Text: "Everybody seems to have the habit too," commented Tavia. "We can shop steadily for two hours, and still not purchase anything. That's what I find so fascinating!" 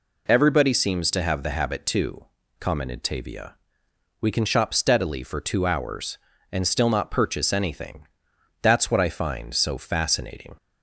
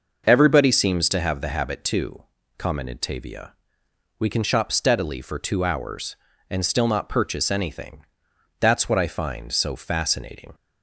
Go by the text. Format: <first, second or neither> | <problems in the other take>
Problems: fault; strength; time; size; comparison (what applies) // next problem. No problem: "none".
first | starts louder than the rest; noticeable; until 1.3 s; 6 dB